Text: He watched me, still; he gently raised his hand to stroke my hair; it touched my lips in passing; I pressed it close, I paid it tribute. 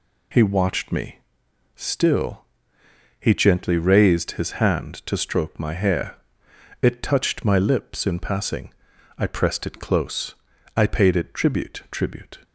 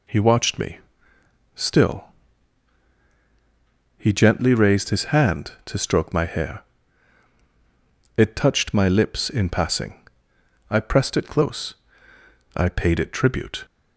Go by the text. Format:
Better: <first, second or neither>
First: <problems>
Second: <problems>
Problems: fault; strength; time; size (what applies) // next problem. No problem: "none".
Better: second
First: says "tribute" twice; at 11.9 s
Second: none